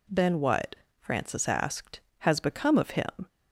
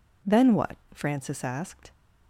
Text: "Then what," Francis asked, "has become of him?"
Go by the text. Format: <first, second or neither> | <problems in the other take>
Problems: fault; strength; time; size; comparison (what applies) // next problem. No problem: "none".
first | stops before "has become of him"; at 1.9 s